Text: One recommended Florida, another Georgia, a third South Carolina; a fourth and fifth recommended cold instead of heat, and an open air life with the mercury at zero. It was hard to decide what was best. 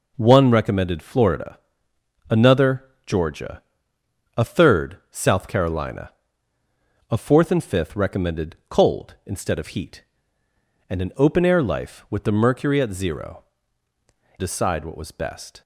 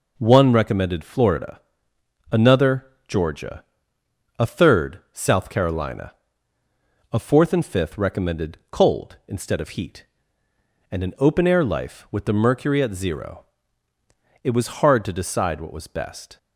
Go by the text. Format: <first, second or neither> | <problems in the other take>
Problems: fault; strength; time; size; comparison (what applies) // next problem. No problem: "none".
second | pauses between "another" and "Georgia"; slight; at 2.8 s; 0.22 s long; slight in the second // skips "It was hard to"; at 13.9 s